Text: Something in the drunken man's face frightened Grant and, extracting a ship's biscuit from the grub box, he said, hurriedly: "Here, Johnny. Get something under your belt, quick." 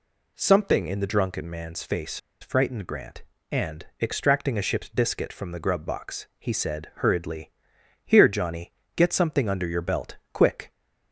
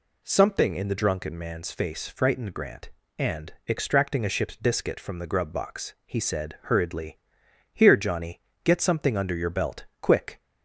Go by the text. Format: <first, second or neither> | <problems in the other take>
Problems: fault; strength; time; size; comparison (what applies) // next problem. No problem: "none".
second | pauses between "face" and "frightened"; slight; at 2.1 s; 0.23 s long